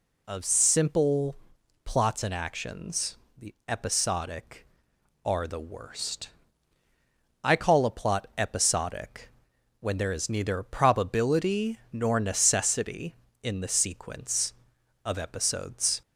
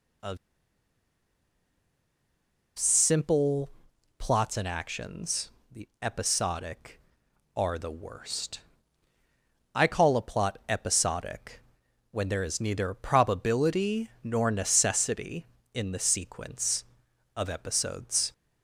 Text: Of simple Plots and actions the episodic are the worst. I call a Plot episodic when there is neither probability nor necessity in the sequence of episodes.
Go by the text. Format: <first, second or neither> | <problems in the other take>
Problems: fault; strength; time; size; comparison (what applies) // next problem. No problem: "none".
first | pauses between "Of" and "simple"; strong; at 0.3 s; 2.4 s long // pauses between "simple" and "Plots"; noticeable; at 3.7 s; 0.48 s long; noticeable in the first // pauses between "actions" and "the"; slight; at 5.5 s; 0.20 s long; slight in the first // pauses between "episodic" and "when"; noticeable; at 11.6 s; 0.52 s long; noticeable in the first